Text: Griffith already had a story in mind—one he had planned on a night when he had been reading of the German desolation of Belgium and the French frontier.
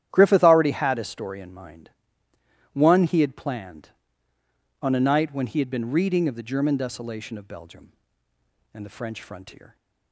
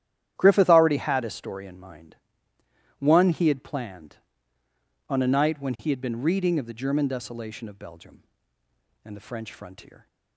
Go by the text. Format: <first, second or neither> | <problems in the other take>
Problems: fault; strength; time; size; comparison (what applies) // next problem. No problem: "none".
neither | starts louder than the rest; strong; the same in both